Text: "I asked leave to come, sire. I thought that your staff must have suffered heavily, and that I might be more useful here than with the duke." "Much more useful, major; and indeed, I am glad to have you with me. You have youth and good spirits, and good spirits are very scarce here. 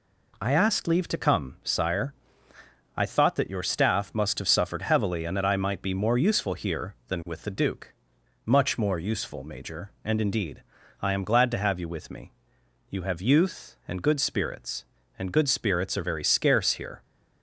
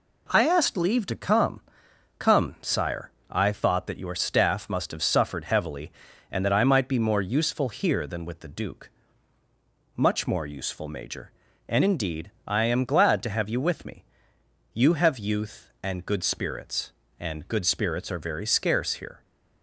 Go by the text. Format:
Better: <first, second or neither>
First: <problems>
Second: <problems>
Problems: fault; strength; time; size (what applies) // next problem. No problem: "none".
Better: first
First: none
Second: says "come" twice; at 2.1 s